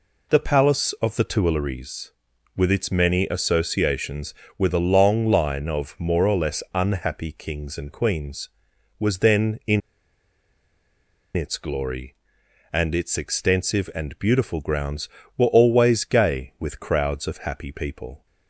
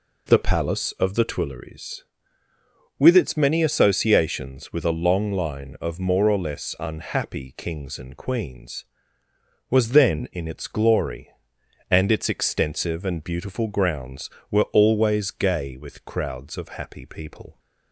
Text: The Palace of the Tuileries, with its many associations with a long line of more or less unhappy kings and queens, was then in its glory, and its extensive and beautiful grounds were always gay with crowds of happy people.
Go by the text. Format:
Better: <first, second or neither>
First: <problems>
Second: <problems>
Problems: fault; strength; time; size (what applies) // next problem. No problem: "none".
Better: second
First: pauses between "in" and "its"; strong; at 9.8 s; 1.5 s long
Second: none